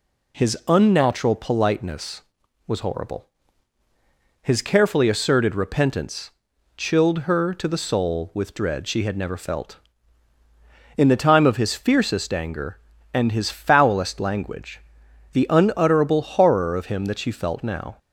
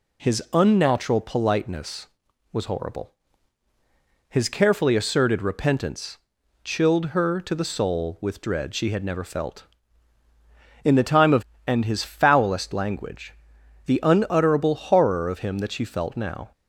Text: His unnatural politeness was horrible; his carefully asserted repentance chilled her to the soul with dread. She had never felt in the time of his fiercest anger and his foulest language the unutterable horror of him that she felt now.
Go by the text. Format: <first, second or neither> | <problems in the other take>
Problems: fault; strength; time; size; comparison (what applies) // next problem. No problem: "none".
first | pauses between "repentance" and "chilled"; at 6.1 s; 0.44 s long; also in the first // skips "his fiercest anger"; at 11.5 s // pauses between "language" and "the"; noticeable; at 13.3 s; 0.54 s long; noticeable in the first